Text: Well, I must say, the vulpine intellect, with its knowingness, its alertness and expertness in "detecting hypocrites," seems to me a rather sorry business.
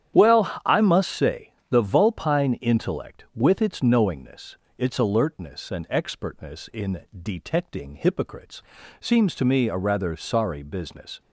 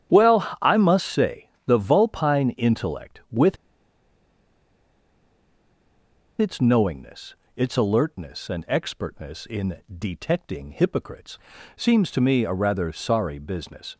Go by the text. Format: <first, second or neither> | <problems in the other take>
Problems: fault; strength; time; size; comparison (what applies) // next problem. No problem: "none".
first | starts louder than the rest; strong; until 1.2 s; 10 dB; strong in the first // pauses between "with" and "its"; strong; at 3.5 s; 2.8 s long // pauses between "in" and "detecting"; slight; at 9.7 s; 0.18 s long; slight in the first